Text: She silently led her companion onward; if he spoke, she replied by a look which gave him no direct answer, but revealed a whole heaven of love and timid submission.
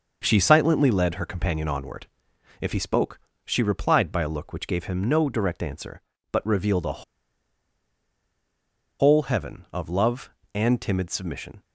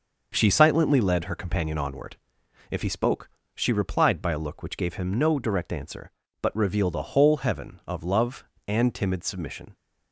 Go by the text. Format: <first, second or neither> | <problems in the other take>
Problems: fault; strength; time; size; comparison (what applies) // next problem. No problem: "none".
second | starts louder than the rest; noticeable; until 1.2 s; 6 dB; noticeable in the second // pauses between "a" and "whole"; strong; at 7.0 s; 1.9 s long